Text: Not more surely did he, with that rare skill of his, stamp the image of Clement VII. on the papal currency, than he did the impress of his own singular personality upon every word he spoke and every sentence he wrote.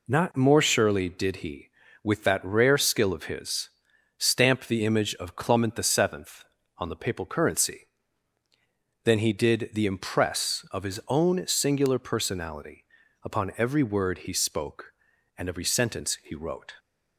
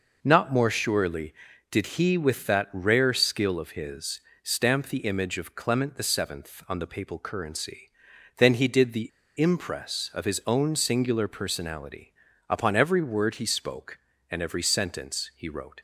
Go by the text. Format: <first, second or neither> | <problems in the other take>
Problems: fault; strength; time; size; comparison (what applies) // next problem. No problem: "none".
first | pauses between "the" and "impress"; slight; at 9.0 s; 0.30 s long // pauses between "personality" and "upon"; slight; at 12.1 s; 0.36 s long; also in the first